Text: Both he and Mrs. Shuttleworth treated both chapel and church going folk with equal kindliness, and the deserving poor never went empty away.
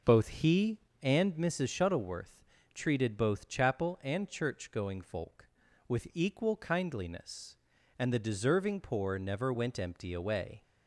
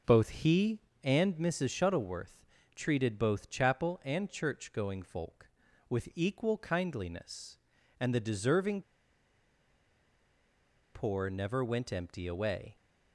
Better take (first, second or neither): first